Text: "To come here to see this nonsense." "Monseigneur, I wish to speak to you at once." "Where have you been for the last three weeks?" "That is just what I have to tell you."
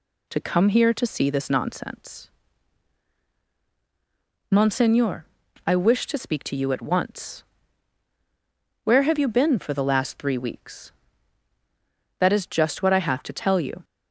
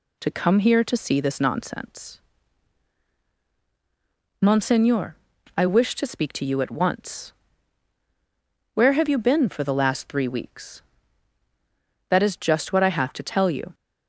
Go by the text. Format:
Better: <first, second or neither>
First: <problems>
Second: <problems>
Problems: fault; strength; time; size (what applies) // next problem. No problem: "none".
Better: neither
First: none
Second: none